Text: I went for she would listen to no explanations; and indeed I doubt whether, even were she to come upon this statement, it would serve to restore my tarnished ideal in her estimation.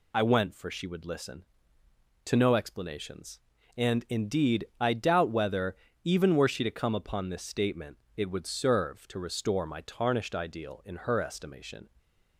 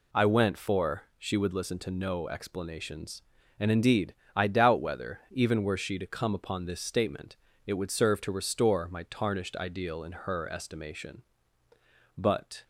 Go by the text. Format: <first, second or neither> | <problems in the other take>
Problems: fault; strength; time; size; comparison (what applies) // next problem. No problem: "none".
first | pauses between "indeed" and "I"; slight; at 4.1 s; 0.22 s long // goes on to say "But"; slight; from 12.1 s on; 0.46 s long